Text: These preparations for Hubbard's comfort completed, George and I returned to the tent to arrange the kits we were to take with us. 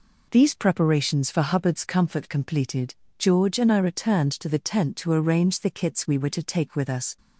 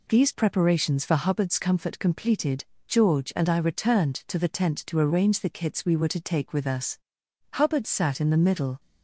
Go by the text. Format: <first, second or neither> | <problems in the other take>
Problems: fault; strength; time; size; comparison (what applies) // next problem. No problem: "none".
first | goes on to say "Hubbard sat in the middle"; noticeable; from 7.5 s on; 1.2 s long